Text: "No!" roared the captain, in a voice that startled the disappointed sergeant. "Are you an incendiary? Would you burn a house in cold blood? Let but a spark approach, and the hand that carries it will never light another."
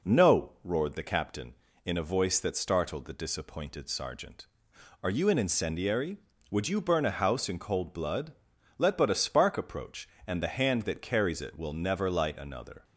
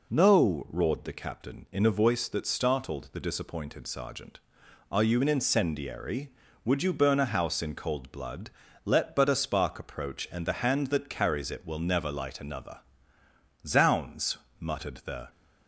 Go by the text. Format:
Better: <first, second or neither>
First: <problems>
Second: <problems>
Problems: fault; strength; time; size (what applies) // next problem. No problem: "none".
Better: first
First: none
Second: goes on to say "Zounds muttered the"; from 13.6 s on; 1.6 s long